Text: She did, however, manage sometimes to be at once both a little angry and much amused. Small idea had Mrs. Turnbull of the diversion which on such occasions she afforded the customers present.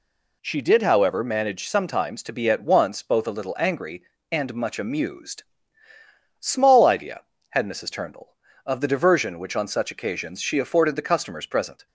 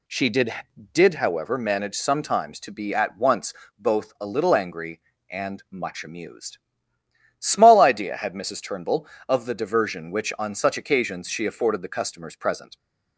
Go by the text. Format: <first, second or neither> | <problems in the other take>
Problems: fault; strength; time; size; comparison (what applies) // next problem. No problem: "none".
first | says "did" twice; at 0.9 s // pauses between "once" and "both"; slight; at 3.5 s; 0.24 s long